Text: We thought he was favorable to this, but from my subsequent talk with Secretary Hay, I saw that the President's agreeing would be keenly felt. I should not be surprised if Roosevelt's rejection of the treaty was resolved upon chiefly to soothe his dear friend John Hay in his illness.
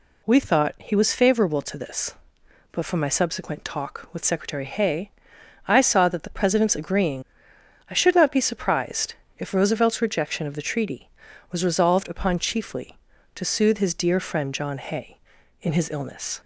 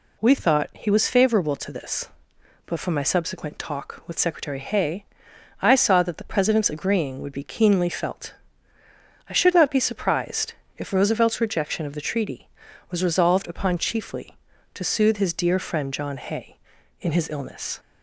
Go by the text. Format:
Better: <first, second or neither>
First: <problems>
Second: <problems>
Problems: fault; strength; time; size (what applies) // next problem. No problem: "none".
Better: second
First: skips "would be keenly felt"; at 7.5 s // pauses between "surprised" and "if"; slight; at 9.1 s; 0.22 s long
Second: pauses between "surprised" and "if"; slight; at 10.5 s; 0.22 s long